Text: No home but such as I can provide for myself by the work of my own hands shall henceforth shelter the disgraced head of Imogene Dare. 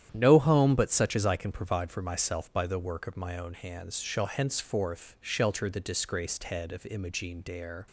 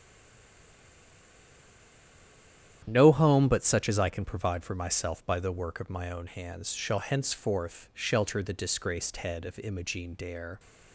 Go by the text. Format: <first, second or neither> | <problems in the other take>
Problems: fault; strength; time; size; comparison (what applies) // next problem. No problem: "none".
first | stays silent before the first word; strong; until 2.8 s; 2.8 s long // starts louder than the rest; strong; until 3.8 s; 10.5 dB; strong in the first